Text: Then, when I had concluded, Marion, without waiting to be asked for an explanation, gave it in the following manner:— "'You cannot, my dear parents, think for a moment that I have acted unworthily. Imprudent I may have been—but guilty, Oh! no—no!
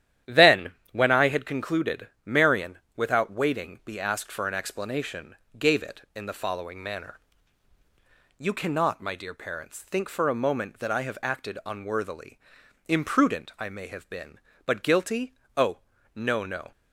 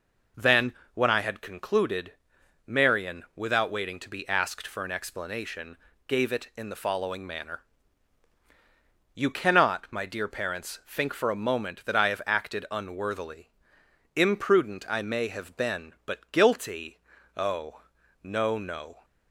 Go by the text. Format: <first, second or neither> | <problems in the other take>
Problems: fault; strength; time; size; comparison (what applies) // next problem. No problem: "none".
second | starts louder than the rest; strong; until 1.4 s; 11 dB // skips "to"; at 3.8 s